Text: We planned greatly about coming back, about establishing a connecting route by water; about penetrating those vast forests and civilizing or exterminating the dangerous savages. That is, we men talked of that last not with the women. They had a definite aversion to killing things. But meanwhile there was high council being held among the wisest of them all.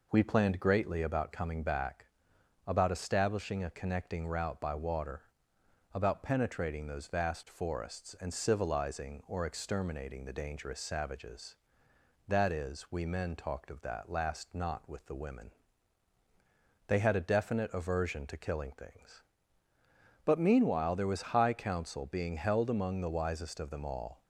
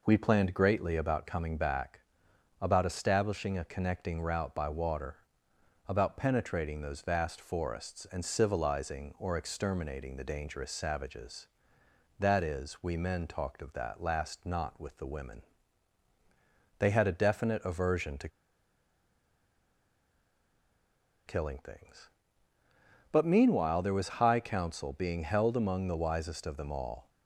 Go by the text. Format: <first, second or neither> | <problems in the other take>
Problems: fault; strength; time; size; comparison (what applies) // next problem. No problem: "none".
first | pauses between "to" and "killing"; strong; at 18.2 s; 2.9 s long